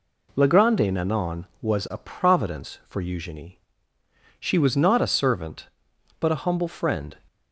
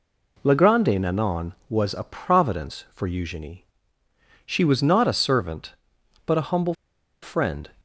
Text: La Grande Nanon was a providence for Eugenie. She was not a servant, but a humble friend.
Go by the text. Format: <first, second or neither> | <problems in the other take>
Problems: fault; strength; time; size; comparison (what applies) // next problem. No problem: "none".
first | pauses between "humble" and "friend"; noticeable; at 6.7 s; 0.47 s long